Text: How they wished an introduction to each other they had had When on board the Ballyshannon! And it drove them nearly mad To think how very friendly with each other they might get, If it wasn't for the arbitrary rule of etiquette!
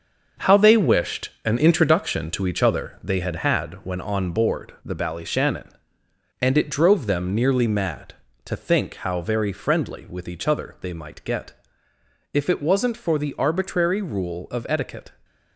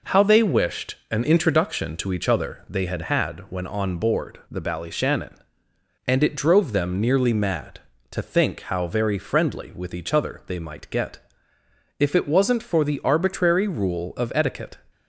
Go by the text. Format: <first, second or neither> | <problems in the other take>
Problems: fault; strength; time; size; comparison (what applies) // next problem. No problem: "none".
second | gets quieter; strong; throughout; 7.5 dB